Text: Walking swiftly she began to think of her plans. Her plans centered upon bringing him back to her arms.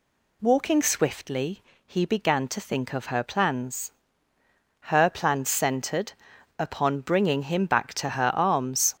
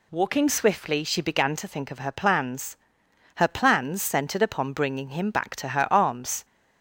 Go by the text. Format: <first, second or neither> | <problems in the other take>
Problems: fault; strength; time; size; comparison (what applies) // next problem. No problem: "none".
second | says "he" for "she"; at 1.8 s // pauses between "centered" and "upon"; noticeable; at 6.1 s; 0.46 s long